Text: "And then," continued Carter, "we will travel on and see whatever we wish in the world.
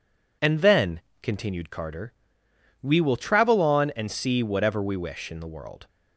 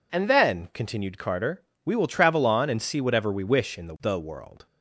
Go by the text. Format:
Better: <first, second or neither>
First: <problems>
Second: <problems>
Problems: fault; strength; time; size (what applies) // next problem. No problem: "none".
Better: first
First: none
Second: says "the" twice; at 4.0 s